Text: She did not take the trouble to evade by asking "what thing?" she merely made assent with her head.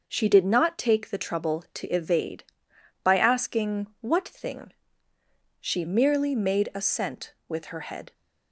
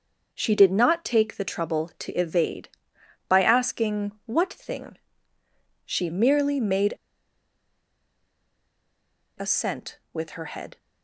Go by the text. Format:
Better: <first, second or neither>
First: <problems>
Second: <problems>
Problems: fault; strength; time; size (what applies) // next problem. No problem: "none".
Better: first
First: none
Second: pauses between "made" and "assent"; strong; at 6.9 s; 2.4 s long